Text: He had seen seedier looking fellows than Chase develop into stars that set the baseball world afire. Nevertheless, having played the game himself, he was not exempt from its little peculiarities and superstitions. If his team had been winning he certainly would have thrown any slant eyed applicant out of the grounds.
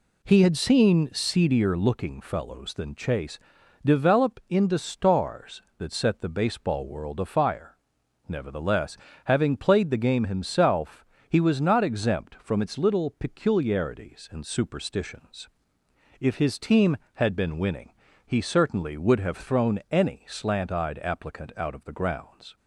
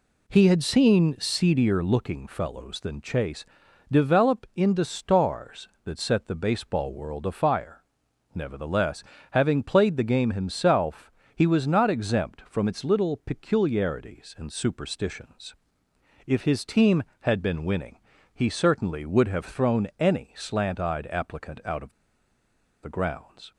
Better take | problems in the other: first | pauses between "Chase" and "develop"; noticeable; at 3.4 s; 0.46 s long; noticeable in the first // pauses between "winning" and "he"; slight; at 17.9 s; 0.36 s long; slight in the first // pauses between "of" and "the"; noticeable; at 21.9 s; 0.89 s long

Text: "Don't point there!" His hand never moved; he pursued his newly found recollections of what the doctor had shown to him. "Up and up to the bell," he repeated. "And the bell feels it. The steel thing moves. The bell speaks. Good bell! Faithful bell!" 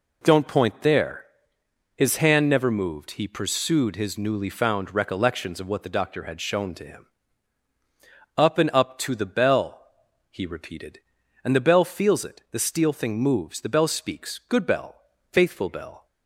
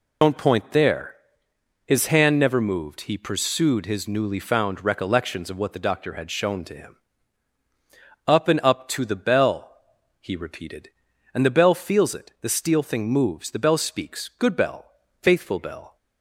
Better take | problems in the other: first | loses the start of "Don't"; at 0.2 s; 90 ms

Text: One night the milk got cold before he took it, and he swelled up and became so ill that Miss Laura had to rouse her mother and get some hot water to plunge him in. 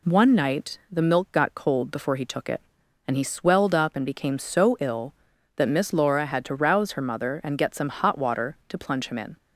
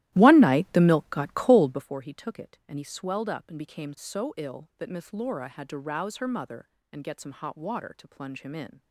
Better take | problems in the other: first | starts louder than the rest; strong; until 1.9 s; 15 dB

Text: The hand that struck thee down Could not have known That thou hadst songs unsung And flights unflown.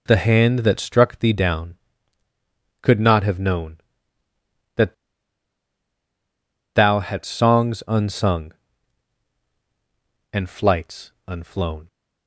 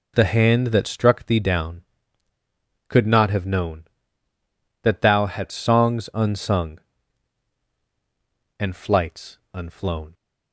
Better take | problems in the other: second | pauses between "That" and "thou"; strong; at 4.9 s; 1.8 s long // pauses between "flights" and "unflown"; slight; at 11.1 s; 0.16 s long; slight in the second

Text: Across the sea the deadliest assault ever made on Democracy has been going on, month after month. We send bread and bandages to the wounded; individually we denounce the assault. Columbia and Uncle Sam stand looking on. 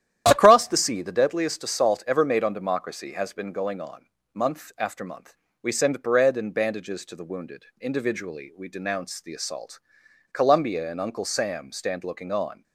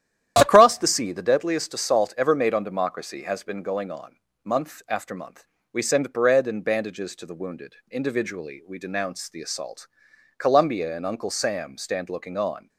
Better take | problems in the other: neither | starts louder than the rest; strong; the same in both

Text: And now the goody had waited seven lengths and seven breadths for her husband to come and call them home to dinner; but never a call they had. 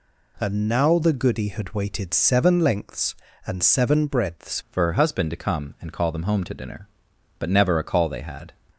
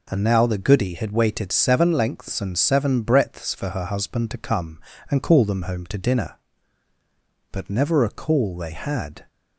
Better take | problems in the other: second | changes voice at "for"; from 4.7 s on; 3.8 s long

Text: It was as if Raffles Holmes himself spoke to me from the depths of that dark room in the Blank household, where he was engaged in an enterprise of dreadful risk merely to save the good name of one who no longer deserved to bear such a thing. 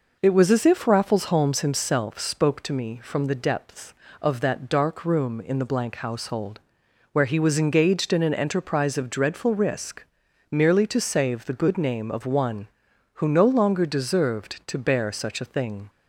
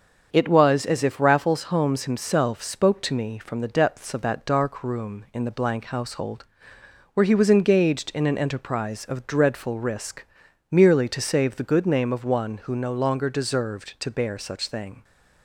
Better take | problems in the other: first | starts louder than the rest; until 1.3 s; 6.5 dB // pauses between "risk" and "merely"; noticeable; at 10.2 s; 0.50 s long; noticeable in the first // skips "a"; at 14.6 s

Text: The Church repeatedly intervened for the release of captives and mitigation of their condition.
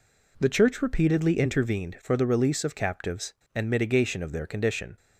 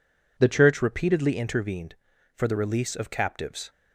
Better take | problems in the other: first | stops before "and mitigation of their condition"; at 3.6 s

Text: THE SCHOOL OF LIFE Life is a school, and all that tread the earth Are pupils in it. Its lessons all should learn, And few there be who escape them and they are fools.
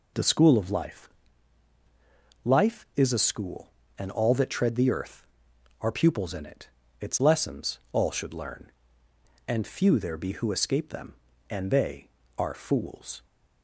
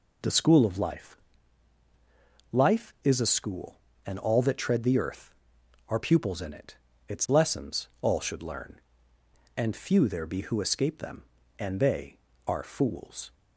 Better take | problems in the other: neither | pauses between "LIFE" and "Life"; strong; the same in both

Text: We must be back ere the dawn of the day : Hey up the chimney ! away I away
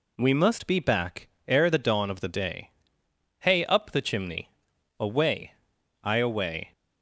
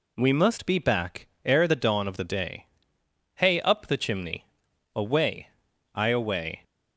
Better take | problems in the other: neither | pauses between "back" and "ere"; slight; the same in both // pauses between "away" and "I"; noticeable; the same in both

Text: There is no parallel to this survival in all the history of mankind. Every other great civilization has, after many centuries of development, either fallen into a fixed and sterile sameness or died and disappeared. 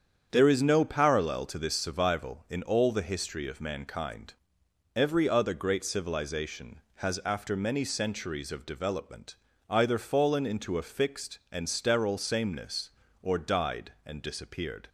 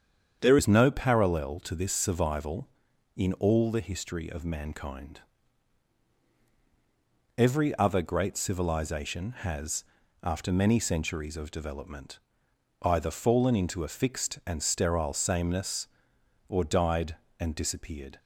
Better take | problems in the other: first | starts louder than the rest; strong; until 1.4 s; 8 dB; strong in the first // changes voice at "is"; from 0.5 s on; 17.6 s long

